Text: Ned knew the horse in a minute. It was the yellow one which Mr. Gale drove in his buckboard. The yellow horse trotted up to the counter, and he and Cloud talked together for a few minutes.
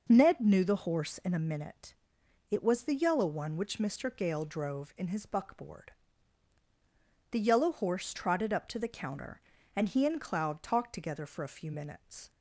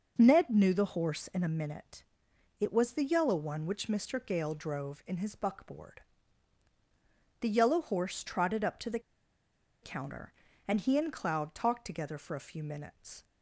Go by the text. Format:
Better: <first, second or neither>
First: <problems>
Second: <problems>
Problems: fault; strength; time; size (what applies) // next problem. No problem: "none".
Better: first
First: none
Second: pauses between "the" and "counter"; noticeable; at 8.9 s; 0.83 s long